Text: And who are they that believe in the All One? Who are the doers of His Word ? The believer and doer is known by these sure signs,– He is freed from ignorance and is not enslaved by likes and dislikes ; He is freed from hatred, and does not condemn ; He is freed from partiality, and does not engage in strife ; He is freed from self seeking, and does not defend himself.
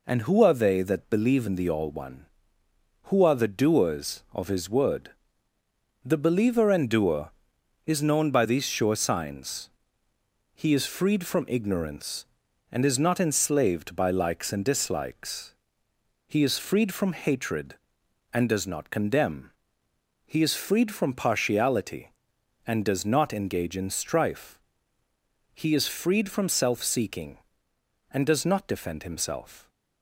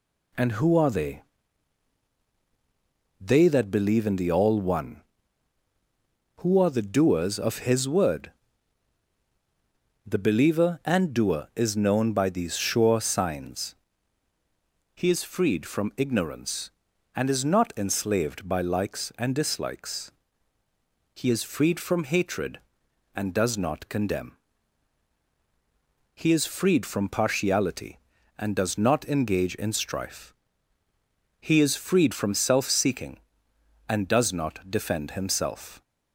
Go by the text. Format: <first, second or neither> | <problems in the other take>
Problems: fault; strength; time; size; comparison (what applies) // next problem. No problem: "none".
first | says "they" twice; at 3.2 s